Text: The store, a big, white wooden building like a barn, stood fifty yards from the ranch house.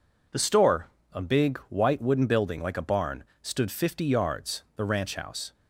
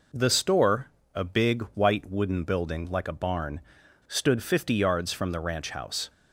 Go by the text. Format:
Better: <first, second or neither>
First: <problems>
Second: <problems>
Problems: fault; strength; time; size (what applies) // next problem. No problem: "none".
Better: second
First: skips "from"; at 4.6 s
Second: none